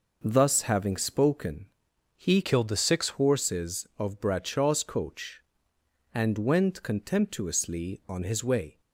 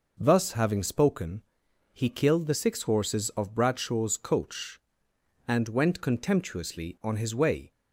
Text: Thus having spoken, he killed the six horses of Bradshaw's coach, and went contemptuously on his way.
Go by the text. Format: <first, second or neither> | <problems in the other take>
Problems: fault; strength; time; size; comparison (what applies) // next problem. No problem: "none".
second | changes voice from "killed" to "six"; from 2.4 to 3.1 s; 0.7 s long